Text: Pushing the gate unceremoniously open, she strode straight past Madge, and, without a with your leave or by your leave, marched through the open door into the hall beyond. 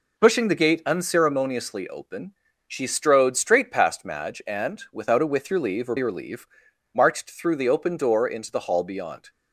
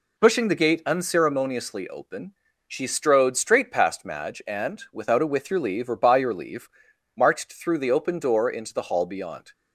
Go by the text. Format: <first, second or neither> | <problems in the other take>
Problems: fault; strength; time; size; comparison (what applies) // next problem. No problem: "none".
second | skips "by"; at 5.9 s